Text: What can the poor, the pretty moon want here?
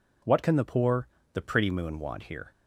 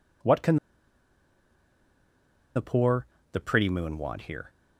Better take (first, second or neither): first